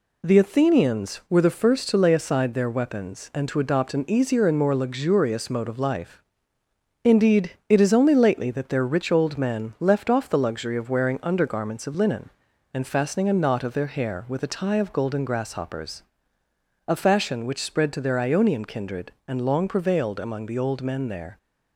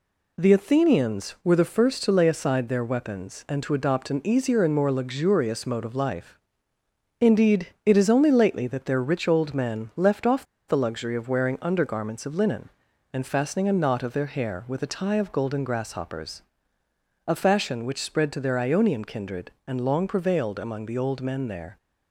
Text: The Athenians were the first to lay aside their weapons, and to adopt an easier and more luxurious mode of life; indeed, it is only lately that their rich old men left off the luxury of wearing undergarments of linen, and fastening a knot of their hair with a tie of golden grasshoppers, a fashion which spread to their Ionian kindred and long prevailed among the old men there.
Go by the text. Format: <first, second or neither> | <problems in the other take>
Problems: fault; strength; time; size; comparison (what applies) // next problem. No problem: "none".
first | pauses between "off" and "the"; slight; at 10.4 s; 0.23 s long